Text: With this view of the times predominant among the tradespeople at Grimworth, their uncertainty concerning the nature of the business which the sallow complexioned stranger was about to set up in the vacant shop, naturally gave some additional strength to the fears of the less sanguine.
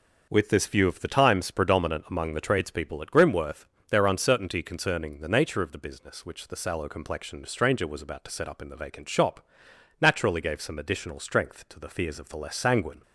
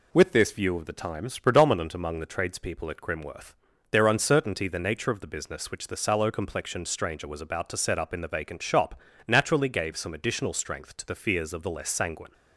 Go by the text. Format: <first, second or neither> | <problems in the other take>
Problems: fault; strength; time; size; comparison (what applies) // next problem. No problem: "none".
first | skips "concerning"; at 4.6 s